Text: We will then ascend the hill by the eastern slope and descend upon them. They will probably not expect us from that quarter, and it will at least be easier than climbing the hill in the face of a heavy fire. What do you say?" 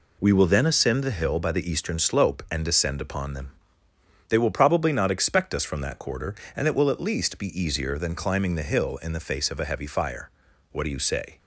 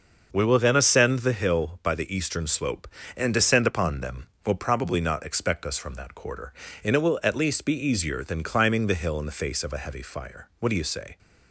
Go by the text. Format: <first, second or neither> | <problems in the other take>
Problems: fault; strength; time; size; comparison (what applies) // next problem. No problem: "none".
first | skips "They"; at 4.3 s